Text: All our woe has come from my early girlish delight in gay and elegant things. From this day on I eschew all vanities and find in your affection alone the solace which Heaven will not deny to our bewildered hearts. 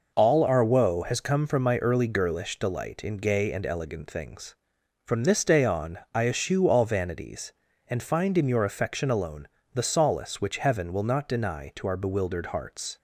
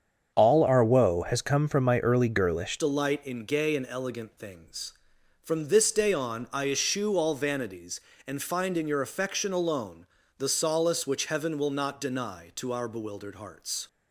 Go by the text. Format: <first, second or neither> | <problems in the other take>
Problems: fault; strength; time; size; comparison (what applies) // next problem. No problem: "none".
first | starts louder than the rest; strong; until 1.3 s; 7.5 dB // changes voice at "delight"; from 2.7 s on; 11.1 s long // pauses between "alone" and "the"; slight; at 10.0 s; 0.32 s long; slight in the first